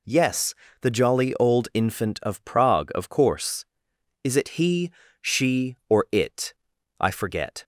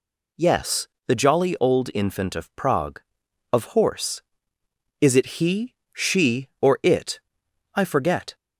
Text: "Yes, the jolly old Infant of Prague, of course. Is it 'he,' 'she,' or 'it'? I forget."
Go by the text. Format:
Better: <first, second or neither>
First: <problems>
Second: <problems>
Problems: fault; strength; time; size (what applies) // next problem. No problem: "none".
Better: first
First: none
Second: says "horse" for "course"; at 3.6 s